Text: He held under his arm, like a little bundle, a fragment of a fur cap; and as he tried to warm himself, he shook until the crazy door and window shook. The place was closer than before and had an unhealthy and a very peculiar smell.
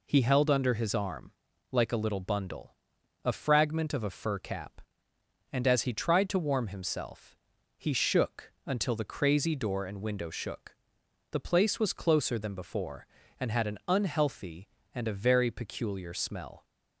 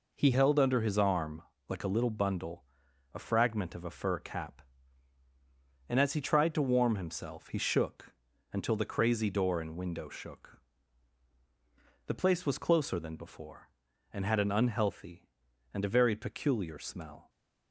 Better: first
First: none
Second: changes voice at "held"; from 0.3 s on; 16.9 s long // pauses between "shook" and "until"; slight; at 8.1 s; 0.36 s long

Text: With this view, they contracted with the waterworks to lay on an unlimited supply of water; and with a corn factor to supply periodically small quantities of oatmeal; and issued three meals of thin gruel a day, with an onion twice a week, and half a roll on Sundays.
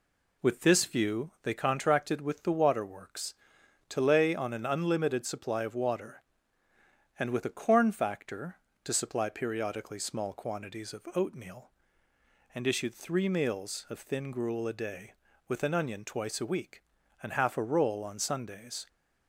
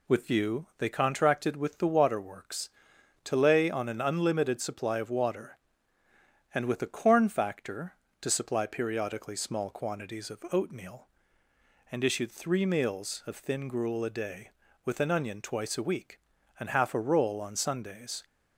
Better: first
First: none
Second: skips "this"; at 0.2 s

